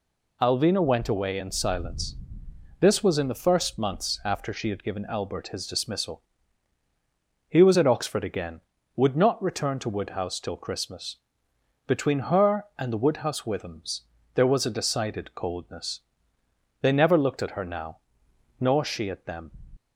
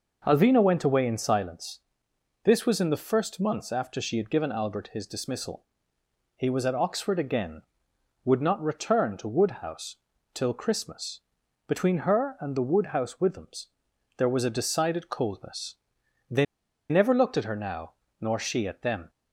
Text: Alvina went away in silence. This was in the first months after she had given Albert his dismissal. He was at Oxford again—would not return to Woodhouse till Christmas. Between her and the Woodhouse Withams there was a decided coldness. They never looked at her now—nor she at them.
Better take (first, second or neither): first